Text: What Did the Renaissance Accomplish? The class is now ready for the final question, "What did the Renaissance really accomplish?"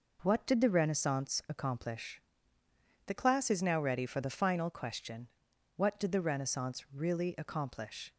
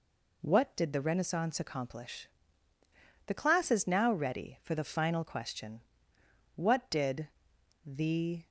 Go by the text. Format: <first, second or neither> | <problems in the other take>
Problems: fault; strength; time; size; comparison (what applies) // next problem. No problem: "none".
first | pauses between "did" and "the"; noticeable; at 7.2 s; 0.56 s long // stops before "Renaissance really accomplish"; at 8.4 s